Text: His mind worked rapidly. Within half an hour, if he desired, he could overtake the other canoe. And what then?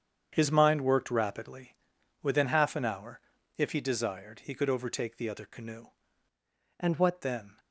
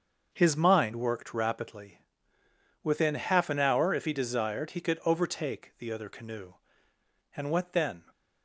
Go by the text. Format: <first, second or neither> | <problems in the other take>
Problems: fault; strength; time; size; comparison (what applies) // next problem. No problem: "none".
second | starts louder than the rest; strong; until 1.3 s; 8 dB; also in the second // changes voice from "And" to "what"; from 6.7 to 7.2 s; 0.5 s long